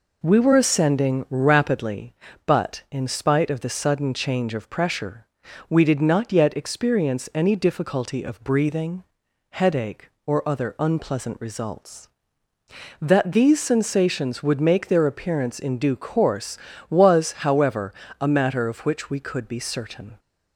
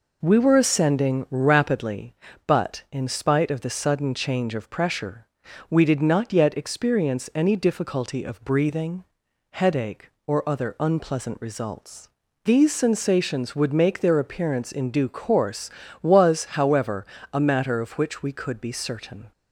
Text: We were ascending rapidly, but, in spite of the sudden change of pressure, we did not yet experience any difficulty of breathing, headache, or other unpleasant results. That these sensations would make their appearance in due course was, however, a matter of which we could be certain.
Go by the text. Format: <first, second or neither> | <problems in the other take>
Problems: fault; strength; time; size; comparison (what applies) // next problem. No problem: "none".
first | skips "That"; at 12.2 s